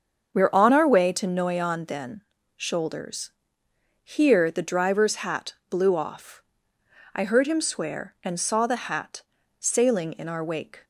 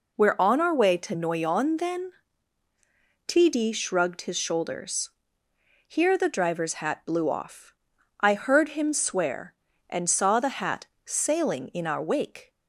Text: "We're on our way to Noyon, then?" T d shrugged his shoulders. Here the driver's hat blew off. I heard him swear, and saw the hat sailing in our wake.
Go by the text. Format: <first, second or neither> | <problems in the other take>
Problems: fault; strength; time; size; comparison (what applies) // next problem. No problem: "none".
second | starts louder than the rest; until 1.4 s; 7 dB // skips "T d shrugged his"; at 2.3 s // pauses between "hat" and "blew"; slight; at 5.5 s; 0.16 s long // pauses between "hat" and "sailing"; slight; at 9.2 s; 0.36 s long; slight in the second